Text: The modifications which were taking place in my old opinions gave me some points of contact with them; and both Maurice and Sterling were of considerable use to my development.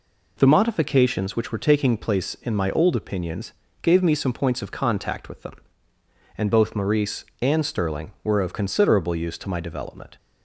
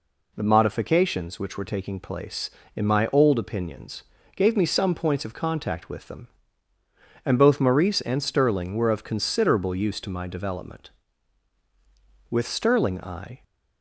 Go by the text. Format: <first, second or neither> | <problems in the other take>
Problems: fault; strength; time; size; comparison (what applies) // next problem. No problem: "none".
first | pauses between "opinions" and "gave"; slight; at 4.0 s; 0.32 s long; slight in the first // goes on to say "With Sterling I"; noticeable; from 12.3 s on; 1.1 s long